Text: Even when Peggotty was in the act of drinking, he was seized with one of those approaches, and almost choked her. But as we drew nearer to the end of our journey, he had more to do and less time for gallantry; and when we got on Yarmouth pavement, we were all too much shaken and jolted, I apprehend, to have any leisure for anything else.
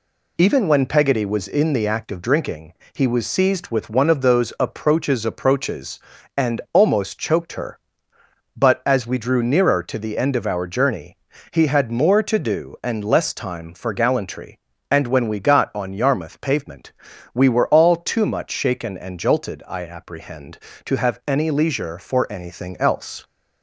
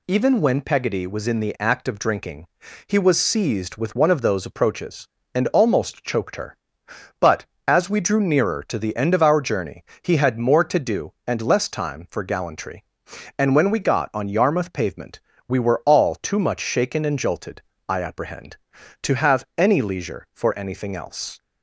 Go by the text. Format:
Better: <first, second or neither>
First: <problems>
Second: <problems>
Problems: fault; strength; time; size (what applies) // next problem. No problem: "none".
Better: second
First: says "approaches" twice; at 5.2 s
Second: none